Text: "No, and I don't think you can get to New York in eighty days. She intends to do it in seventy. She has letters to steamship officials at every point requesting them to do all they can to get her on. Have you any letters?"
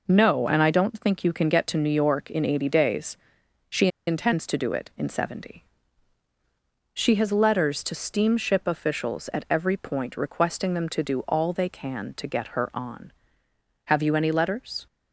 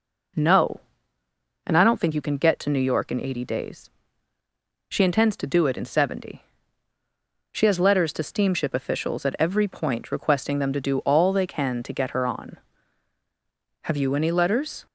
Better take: second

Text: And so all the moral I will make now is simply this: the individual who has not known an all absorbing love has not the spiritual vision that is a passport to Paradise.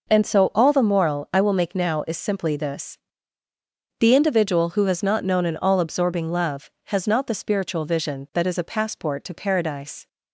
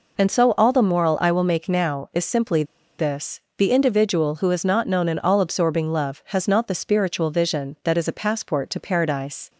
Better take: first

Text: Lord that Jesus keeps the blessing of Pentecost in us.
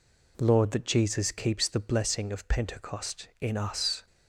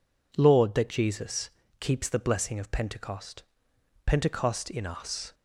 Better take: first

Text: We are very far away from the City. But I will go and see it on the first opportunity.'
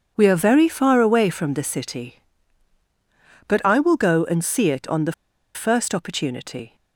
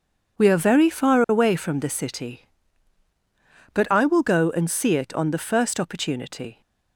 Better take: second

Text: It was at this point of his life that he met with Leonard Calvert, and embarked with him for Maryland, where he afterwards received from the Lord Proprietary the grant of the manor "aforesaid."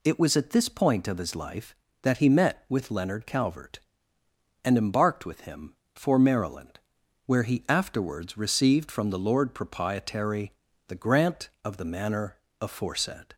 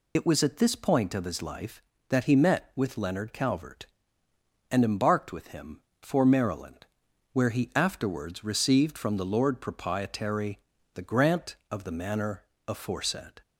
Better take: first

